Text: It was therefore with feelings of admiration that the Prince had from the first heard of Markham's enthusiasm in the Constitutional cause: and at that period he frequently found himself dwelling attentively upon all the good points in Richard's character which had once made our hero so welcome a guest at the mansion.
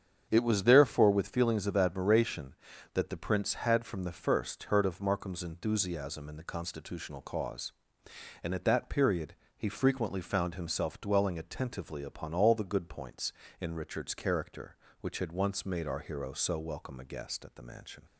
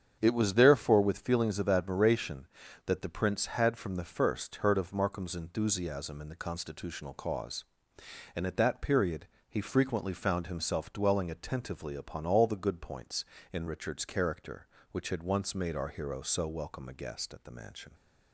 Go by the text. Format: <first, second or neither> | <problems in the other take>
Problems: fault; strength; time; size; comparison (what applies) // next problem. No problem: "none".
neither | starts louder than the rest; strong; the same in both // pauses between "period" and "he"; slight; the same in both